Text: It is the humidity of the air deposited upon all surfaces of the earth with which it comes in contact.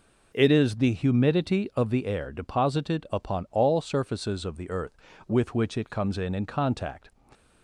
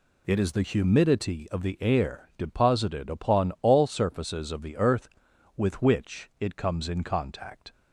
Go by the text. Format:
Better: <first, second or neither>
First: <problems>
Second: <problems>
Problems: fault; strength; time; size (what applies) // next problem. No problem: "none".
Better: second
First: says "in" twice; at 6.3 s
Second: none